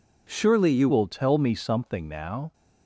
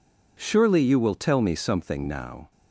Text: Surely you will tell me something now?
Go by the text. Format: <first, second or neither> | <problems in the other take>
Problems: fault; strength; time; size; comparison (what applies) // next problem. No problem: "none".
second | changes voice at "will"; from 0.8 s on; 1.7 s long